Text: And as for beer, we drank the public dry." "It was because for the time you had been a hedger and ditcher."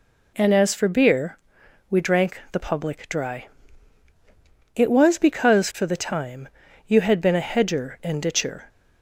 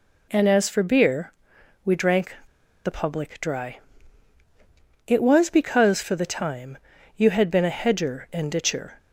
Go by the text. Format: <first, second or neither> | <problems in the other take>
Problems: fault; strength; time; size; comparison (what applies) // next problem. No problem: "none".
first | pauses between "drank" and "the"; noticeable; at 2.3 s; 0.49 s long // pauses between "time" and "you"; at 6.7 s; 0.38 s long; also in the first